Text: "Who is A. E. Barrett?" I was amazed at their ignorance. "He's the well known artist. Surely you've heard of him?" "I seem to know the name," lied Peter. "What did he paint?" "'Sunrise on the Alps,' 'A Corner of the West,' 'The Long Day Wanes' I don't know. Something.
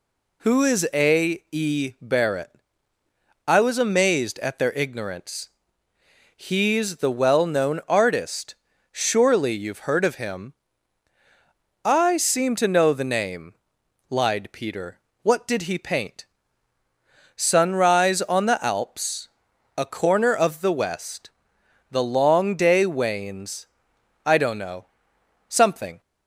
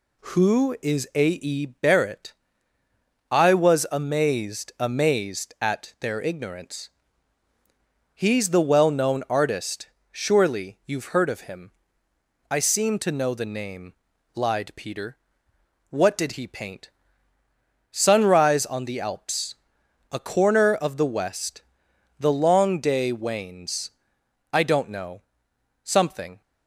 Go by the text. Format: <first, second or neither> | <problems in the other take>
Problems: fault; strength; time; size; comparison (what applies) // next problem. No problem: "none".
first | says "amazed" twice; at 4.7 s // pauses between "Wanes" and "I"; noticeable; at 23.9 s; 0.62 s long; noticeable in the first